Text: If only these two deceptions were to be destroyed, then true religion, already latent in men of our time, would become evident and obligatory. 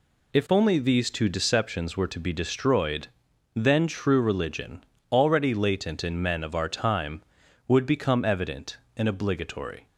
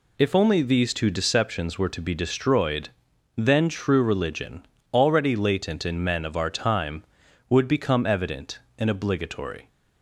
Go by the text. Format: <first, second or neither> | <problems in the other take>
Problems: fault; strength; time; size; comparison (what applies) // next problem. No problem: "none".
neither | none